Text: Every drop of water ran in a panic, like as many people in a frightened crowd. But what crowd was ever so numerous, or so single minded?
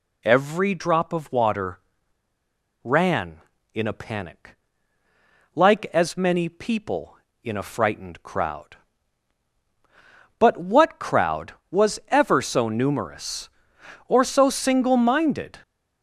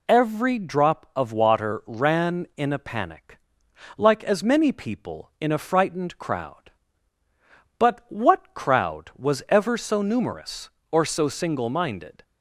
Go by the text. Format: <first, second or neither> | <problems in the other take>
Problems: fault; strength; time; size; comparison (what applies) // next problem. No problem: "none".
second | pauses between "water" and "ran"; at 1.7 s; 1.0 s long